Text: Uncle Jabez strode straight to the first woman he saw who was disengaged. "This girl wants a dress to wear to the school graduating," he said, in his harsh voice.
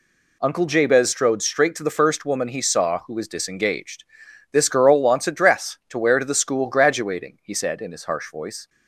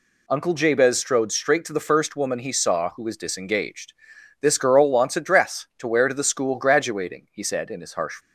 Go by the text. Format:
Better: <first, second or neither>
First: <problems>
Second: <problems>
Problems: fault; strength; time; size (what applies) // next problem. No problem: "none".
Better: first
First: none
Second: stops before "voice"; at 8.2 s